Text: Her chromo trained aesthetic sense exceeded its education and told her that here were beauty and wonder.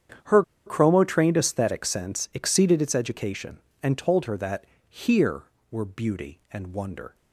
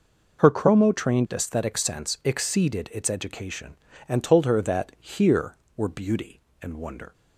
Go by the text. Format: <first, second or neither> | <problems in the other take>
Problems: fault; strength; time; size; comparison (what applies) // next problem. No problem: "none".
second | starts louder than the rest; strong; until 1.4 s; 8.5 dB // pauses between "Her" and "chromo"; slight; at 0.4 s; 0.23 s long // pauses between "that" and "here"; slight; at 4.6 s; 0.24 s long